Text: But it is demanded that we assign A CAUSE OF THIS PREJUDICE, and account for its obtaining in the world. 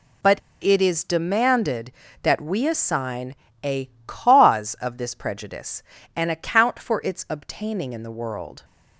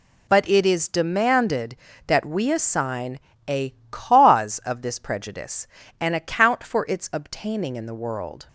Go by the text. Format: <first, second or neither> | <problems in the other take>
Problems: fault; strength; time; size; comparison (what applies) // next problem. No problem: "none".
second | pauses between "But" and "it"; slight; at 0.3 s; 0.24 s long // pauses between "assign" and "A"; slight; at 3.3 s; 0.30 s long; slight in the second // pauses between "A" and "CAUSE"; slight; at 3.8 s; 0.20 s long; slight in the second